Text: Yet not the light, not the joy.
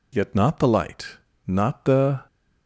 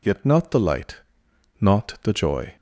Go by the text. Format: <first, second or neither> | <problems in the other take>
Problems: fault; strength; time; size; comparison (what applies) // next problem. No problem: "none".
second | stops before "joy"; at 2.2 s